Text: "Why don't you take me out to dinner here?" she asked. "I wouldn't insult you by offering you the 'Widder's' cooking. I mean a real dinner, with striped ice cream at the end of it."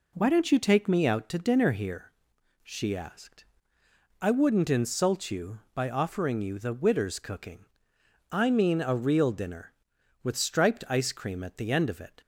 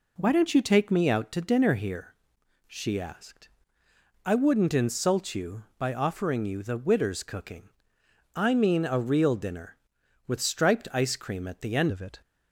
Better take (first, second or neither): first